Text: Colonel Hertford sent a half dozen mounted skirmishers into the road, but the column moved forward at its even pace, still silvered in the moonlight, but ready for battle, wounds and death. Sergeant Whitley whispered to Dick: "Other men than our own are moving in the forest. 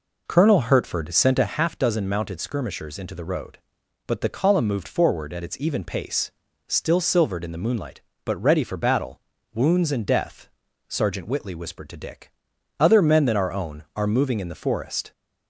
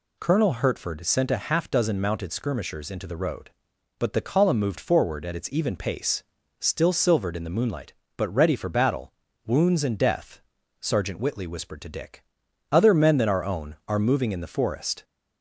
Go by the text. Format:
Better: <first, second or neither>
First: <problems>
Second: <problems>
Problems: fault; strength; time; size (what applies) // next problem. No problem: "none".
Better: second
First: starts louder than the rest; noticeable; until 1.7 s; 4.5 dB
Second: none